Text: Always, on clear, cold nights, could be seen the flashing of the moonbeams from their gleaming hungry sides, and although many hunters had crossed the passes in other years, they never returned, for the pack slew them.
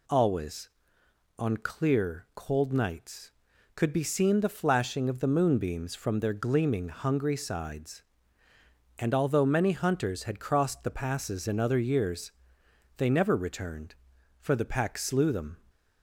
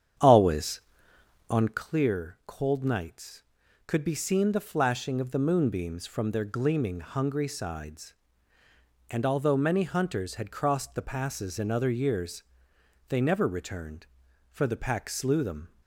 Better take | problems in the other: first | starts louder than the rest; strong; until 1.8 s; 8.5 dB

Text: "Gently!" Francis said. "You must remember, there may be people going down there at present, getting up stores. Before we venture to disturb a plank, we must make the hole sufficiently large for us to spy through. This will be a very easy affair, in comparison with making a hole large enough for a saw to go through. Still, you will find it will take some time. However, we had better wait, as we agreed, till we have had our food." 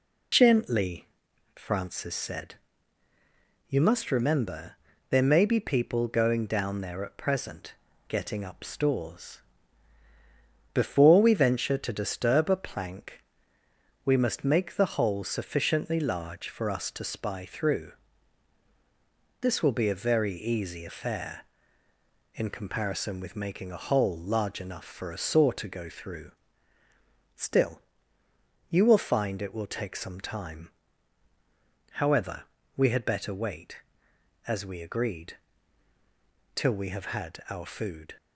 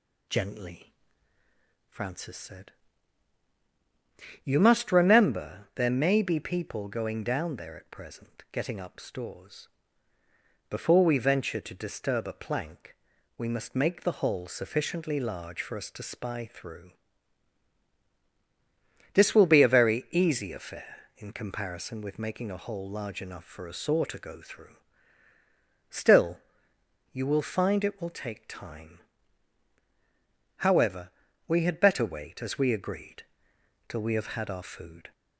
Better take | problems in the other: first | skips "some"; at 28.4 s

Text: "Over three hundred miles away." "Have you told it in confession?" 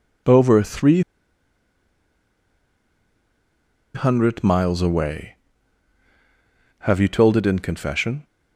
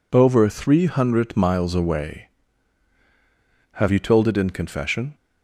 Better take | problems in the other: second | pauses between "three" and "hundred"; strong; at 1.0 s; 2.9 s long

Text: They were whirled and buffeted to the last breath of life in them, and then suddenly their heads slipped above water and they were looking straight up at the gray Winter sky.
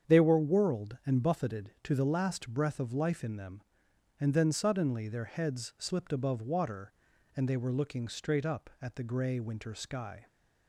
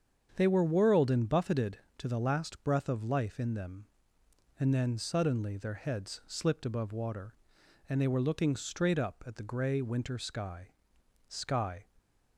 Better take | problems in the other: first | starts louder than the rest; strong; until 1.3 s; 7.5 dB; strong in the first // says "sky" twice; at 11.2 s

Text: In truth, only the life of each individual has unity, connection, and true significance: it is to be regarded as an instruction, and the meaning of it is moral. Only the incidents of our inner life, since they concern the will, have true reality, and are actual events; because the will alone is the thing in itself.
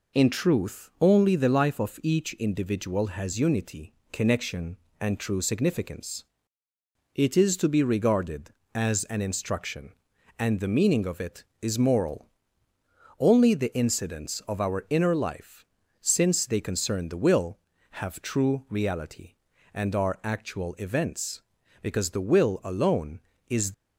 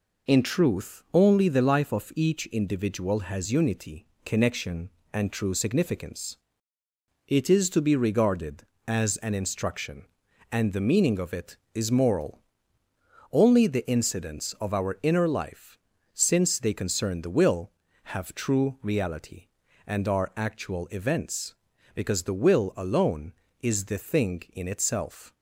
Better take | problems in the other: second | stops before "the thing in itself"; at 23.7 s

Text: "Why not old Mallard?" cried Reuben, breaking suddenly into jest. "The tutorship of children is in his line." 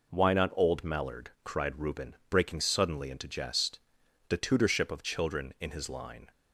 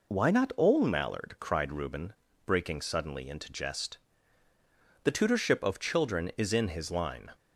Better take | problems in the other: second | skips "is"; at 5.5 s

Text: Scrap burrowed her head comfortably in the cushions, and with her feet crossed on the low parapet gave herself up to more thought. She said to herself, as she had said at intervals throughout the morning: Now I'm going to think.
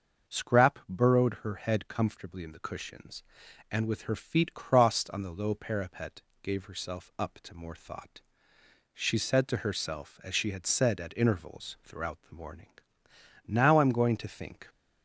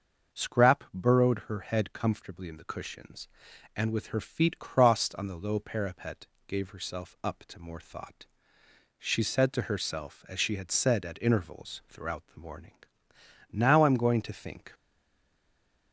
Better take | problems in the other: first | starts louder than the rest; until 1.4 s; 6.5 dB; also in the first // pauses between "parapet" and "gave"; slight; at 6.2 s; 0.22 s long; slight in the first // stays silent after the last word; noticeable; from 14.7 s on; 1.2 s long

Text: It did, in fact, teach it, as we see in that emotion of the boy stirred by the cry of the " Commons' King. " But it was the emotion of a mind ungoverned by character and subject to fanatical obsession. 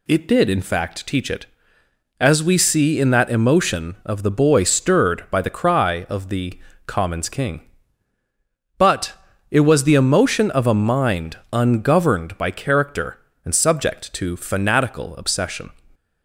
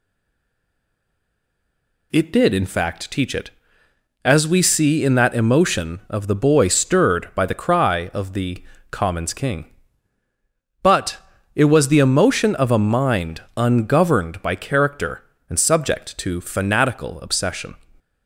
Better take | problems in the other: first | stays silent before the first word; until 2.1 s; 2.1 s long // pauses between "But" and "it"; at 11.1 s; 0.38 s long; also in the first

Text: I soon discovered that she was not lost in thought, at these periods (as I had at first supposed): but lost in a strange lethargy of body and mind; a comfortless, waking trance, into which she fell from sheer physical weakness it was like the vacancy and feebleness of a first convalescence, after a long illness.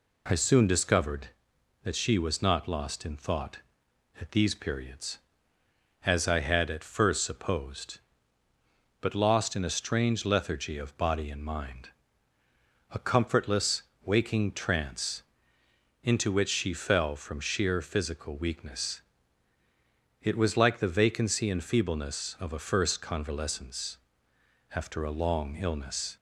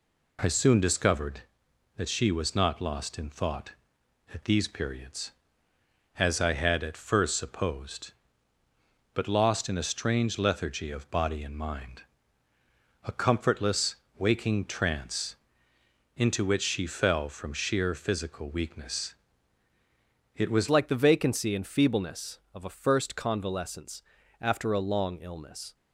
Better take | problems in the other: first | pauses between "weakness" and "it"; at 19.1 s; 1.1 s long; also in the first // changes voice at "like"; from 20.6 s on; 5.1 s long

